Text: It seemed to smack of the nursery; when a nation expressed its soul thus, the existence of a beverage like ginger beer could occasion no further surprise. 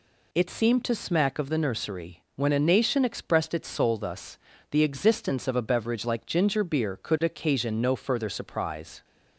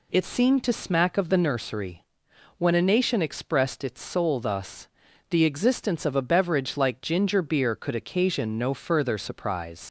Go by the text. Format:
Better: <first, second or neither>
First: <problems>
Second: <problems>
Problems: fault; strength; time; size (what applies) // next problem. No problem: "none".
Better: first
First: none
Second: leaves "surprise" unfinished; at 9.8 s; 105 ms